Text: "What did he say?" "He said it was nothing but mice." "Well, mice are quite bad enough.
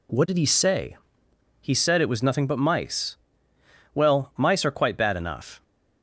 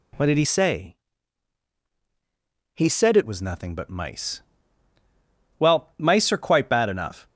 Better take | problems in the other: first | changes voice from "say" to "it"; from 0.4 to 3.2 s; 2.8 s long

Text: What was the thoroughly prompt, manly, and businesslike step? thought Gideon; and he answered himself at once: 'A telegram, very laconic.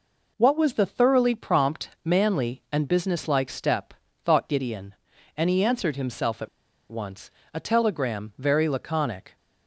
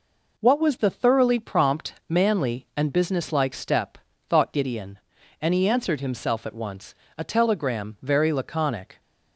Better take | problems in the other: second | pauses between "at" and "once"; at 6.4 s; 0.41 s long

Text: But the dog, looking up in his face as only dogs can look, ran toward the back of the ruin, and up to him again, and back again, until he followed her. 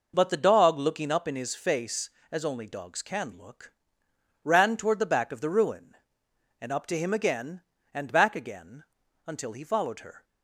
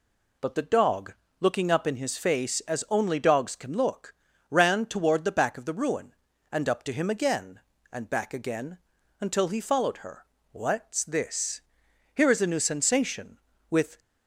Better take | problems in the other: first | goes on to say "What's this Here is a new sensation with"; strong; from 10.5 s on; 3.4 s long

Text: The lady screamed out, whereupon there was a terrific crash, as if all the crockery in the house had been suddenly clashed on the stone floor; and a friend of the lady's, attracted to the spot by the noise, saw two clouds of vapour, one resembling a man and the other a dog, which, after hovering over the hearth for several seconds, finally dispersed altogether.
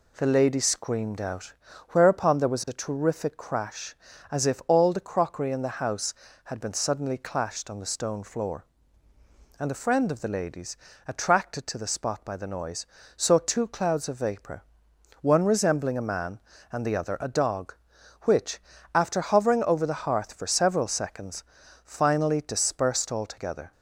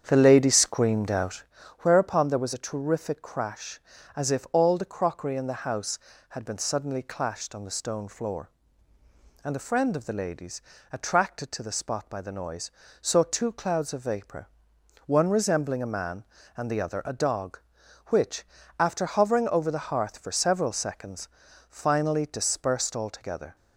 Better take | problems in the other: first | starts louder than the rest; strong; until 1.6 s; 8 dB

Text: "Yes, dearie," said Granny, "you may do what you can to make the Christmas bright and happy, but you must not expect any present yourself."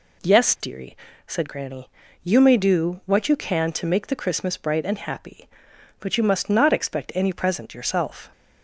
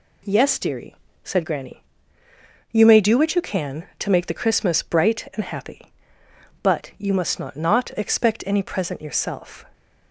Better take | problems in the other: first | says "not" twice; at 7.5 s

